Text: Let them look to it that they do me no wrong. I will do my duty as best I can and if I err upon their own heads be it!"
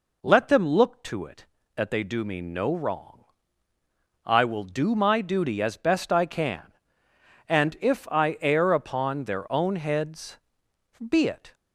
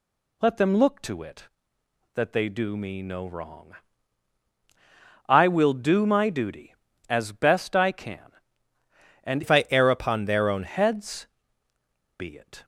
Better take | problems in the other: first | changes voice from "if" to "own"; from 9.4 to 10.6 s; 1.2 s long // pauses between "heads" and "be"; noticeable; at 11.2 s; 0.90 s long; noticeable in the first

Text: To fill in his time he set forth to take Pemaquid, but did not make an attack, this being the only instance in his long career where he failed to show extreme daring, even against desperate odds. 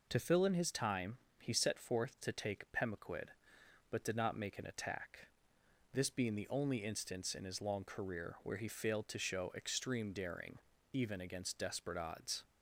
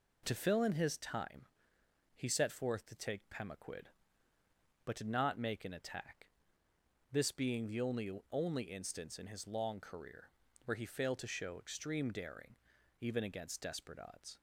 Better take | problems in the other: first | pauses between "time" and "he"; noticeable; at 1.4 s; 0.72 s long; slight in the first // says "only" twice; at 8.3 s // pauses between "career" and "where"; slight; at 10.3 s; 0.34 s long

